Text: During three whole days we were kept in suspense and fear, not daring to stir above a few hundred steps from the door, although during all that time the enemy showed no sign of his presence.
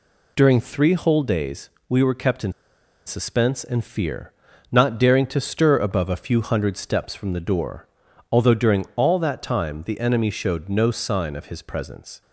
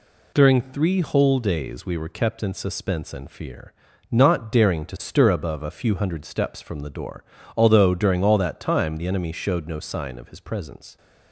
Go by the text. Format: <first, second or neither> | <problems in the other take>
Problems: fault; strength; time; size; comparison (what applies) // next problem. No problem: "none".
second | pauses between "days" and "we"; slight; at 1.6 s; 0.20 s long // pauses between "in" and "suspense"; noticeable; at 2.5 s; 0.54 s long